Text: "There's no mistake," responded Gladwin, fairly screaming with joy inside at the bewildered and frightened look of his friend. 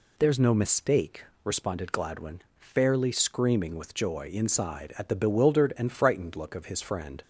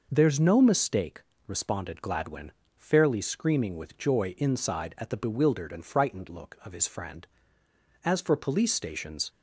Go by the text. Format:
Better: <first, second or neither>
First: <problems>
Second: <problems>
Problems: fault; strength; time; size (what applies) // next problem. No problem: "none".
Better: first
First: none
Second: goes on to say "As for police stations"; noticeable; from 8.0 s on; 1.2 s long